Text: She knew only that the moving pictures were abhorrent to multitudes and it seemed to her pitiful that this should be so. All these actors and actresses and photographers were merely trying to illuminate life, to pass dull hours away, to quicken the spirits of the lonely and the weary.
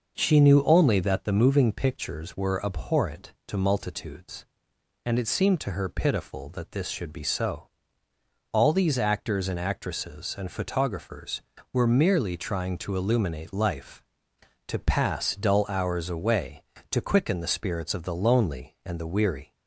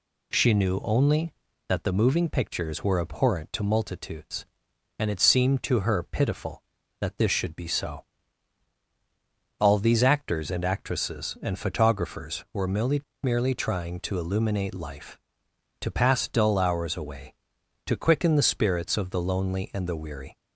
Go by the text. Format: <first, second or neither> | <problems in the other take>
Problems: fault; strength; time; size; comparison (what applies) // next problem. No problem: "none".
first | says "merely" twice; at 13.2 s